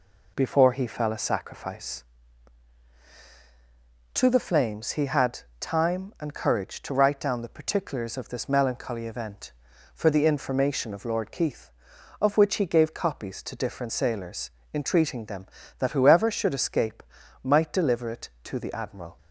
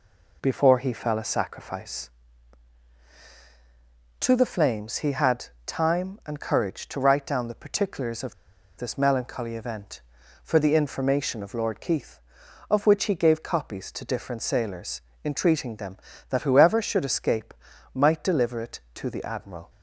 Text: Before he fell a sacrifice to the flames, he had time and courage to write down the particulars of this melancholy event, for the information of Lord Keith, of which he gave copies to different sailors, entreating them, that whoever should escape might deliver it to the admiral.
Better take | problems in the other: first | pauses between "had" and "time"; slight; at 5.4 s; 0.22 s long; slight in the first // pauses between "of" and "this"; at 8.3 s; 0.43 s long // pauses between "escape" and "might"; at 17.5 s; 0.40 s long; also in the first

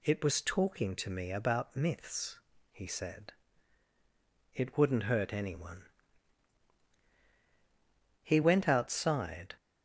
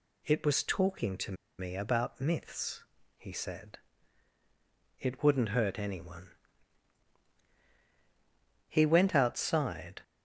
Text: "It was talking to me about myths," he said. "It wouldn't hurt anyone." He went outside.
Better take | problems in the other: first | pauses between "to" and "me"; slight; at 1.3 s; 0.25 s long

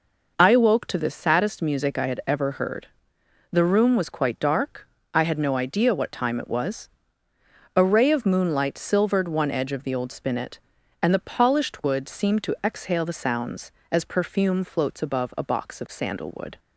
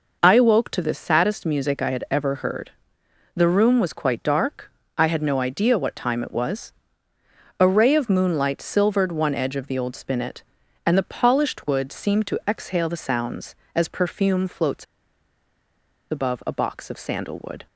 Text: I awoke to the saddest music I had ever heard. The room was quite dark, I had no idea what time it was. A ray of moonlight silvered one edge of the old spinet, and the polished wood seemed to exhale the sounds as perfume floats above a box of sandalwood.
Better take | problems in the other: first | pauses between "floats" and "above"; strong; at 14.8 s; 1.2 s long

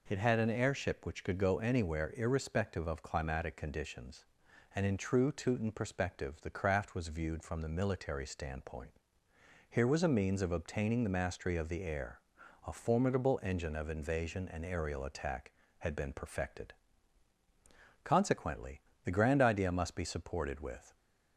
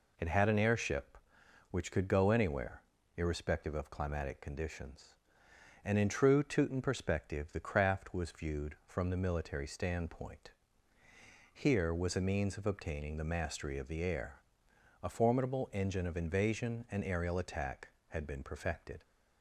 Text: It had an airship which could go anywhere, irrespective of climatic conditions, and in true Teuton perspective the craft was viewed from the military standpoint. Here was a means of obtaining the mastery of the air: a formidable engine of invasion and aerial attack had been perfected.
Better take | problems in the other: second | goes on to say "Consequently the Grand Idea must be supported with"; strong; from 18.0 s on; 2.9 s long

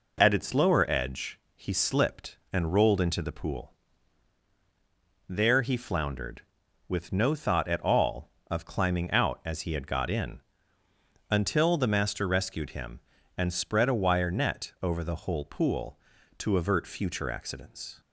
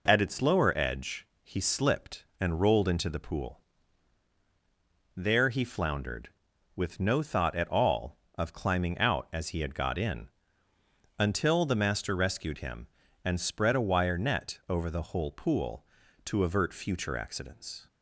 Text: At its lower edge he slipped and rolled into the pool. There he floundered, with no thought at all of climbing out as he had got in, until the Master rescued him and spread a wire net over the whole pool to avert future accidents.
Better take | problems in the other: neither | pauses between "edge" and "he"; slight; the same in both

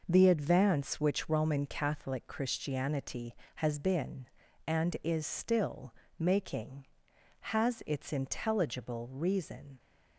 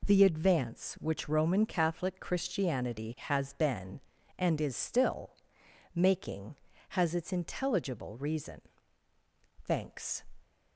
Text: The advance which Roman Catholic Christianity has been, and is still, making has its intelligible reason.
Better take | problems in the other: first | goes on to say "Thanks"; from 9.6 s on; 0.58 s long

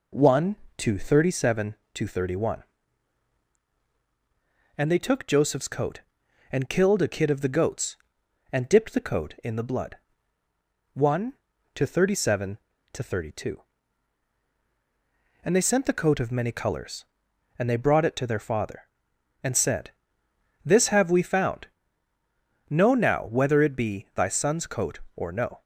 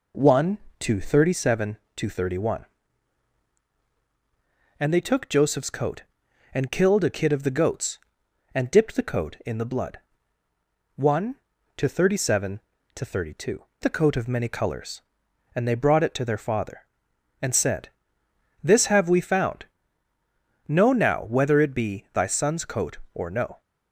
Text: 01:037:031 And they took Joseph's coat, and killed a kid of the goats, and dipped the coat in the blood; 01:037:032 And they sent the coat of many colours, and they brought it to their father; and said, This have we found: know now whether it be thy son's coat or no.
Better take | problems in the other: first | skips "And they sent"; at 13.7 s

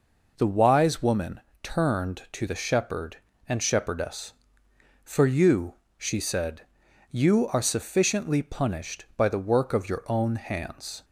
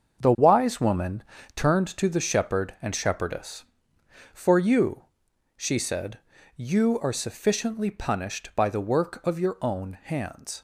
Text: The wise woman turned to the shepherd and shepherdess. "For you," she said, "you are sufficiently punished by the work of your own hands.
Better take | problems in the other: first | gets quieter; strong; throughout; 9 dB // pauses between "woman" and "turned"; slight; at 1.2 s; 0.32 s long; slight in the first

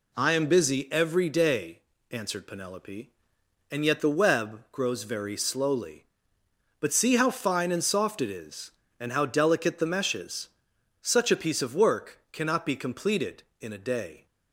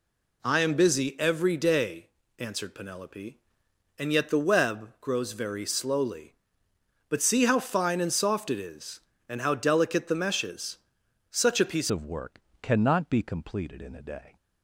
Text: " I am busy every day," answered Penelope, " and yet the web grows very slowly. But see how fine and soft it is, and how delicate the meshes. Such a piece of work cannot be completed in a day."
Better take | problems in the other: first | changes voice at "of"; from 11.8 s on; 2.5 s long // pauses between "work" and "cannot"; slight; at 12.3 s; 0.22 s long

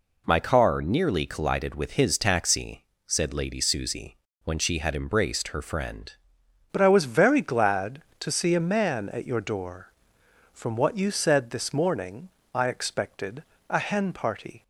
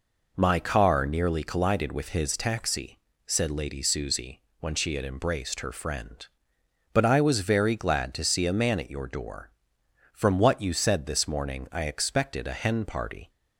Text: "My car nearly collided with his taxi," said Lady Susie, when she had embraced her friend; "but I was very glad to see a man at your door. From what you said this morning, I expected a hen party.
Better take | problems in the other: second | changes voice at "but"; from 6.7 s on; 7.9 s long // pauses between "expected" and "a"; slight; at 13.4 s; 0.26 s long

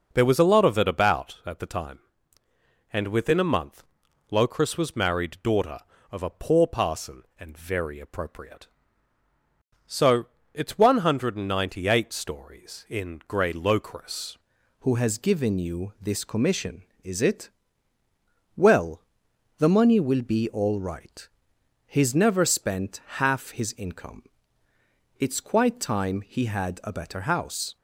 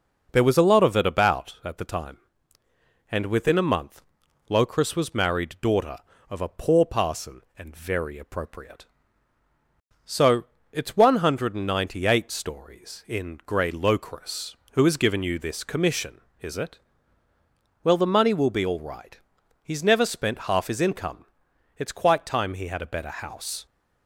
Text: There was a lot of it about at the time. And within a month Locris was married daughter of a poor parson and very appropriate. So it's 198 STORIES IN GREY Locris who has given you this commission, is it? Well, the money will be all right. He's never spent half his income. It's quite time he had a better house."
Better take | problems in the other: second | pauses between "month" and "Locris"; noticeable; at 3.8 s; 0.46 s long; noticeable in the second // pauses between "So" and "it's"; slight; at 10.2 s; 0.28 s long; slight in the second // changes voice at "who"; from 14.8 s on; 12.9 s long

